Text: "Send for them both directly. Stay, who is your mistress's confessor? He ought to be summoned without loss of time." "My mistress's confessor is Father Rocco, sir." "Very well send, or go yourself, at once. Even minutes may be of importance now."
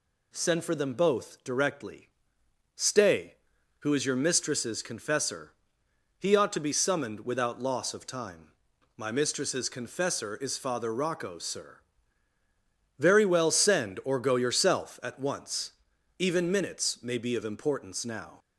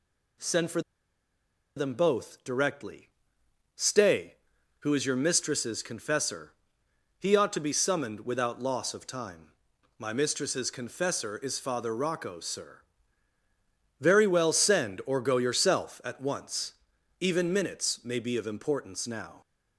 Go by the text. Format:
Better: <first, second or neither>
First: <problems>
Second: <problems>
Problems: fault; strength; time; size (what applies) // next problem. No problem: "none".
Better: first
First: none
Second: pauses between "for" and "them"; noticeable; at 0.8 s; 0.95 s long